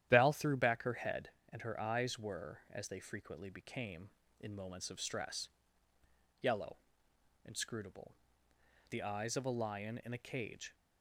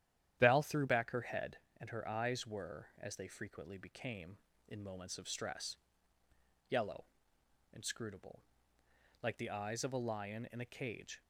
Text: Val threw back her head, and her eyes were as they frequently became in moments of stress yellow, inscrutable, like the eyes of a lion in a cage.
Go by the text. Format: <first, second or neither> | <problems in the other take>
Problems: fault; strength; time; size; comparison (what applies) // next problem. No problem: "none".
second | starts louder than the rest; strong; until 1.1 s; 11 dB; strong in the second // pauses between "stress" and "yellow"; noticeable; at 5.4 s; 0.94 s long; noticeable in the second // skips "like"; at 8.5 s